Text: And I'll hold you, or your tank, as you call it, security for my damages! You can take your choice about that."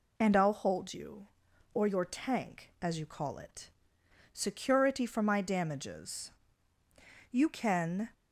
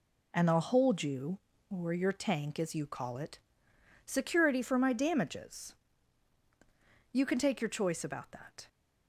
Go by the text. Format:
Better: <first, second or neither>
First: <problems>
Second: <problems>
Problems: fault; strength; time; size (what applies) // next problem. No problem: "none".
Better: second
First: stops before "take your choice about that"; at 8.1 s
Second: none